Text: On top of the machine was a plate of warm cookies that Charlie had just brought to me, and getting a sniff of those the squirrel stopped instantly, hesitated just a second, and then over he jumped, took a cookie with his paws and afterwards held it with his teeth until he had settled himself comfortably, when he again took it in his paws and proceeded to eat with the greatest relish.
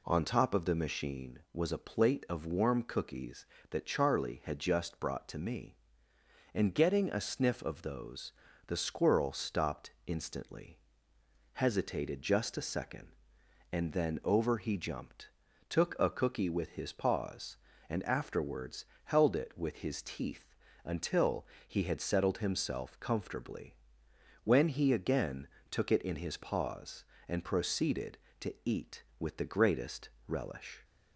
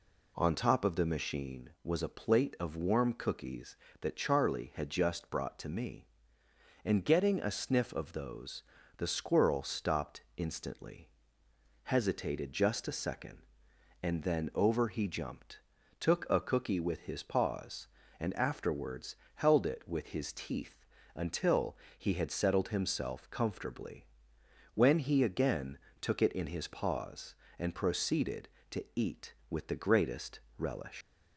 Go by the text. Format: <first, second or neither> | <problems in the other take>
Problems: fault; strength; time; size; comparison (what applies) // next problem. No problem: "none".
first | pauses between "those" and "the"; slight; at 8.6 s; 0.34 s long; slight in the first // pauses between "afterwards" and "held"; slight; at 19.1 s; 0.20 s long; slight in the first // pauses between "teeth" and "until"; slight; at 20.8 s; 0.30 s long; slight in the first // pauses between "until" and "he"; slight; at 21.7 s; 0.20 s long; slight in the first // pauses between "again" and "took"; slight; at 25.7 s; 0.22 s long; slight in the first // pauses between "greatest" and "relish"; slight; at 30.4 s; 0.18 s long; slight in the first // leaves "relish" unfinished; at 31.0 s; 135 ms